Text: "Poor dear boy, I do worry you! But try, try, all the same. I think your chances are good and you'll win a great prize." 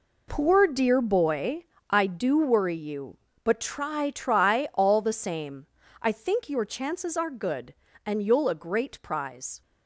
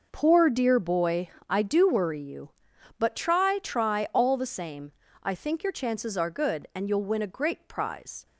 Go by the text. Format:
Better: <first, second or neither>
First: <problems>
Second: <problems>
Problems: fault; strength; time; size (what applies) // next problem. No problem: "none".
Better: second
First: skips "win"; at 8.4 s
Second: none